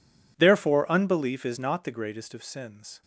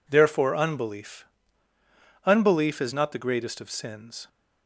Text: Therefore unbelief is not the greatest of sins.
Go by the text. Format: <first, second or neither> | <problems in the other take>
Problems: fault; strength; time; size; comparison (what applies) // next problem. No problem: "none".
first | says "unbelief" twice; at 2.2 s